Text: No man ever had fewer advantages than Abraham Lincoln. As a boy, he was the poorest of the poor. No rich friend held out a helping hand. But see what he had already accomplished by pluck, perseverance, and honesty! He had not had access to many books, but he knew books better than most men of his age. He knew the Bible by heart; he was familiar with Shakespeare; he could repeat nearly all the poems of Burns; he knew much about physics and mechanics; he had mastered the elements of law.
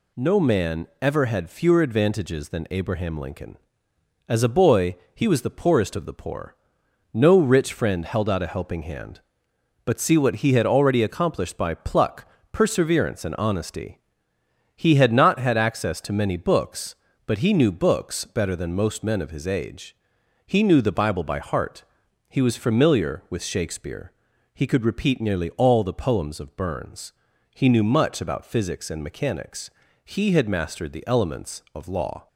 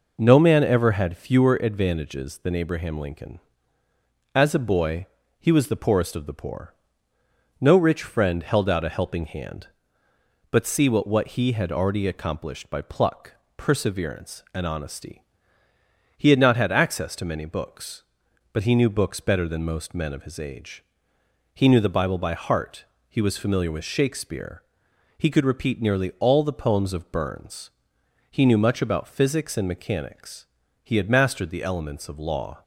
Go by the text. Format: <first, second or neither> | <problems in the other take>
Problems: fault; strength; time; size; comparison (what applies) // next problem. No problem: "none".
first | says "what" twice; at 11.0 s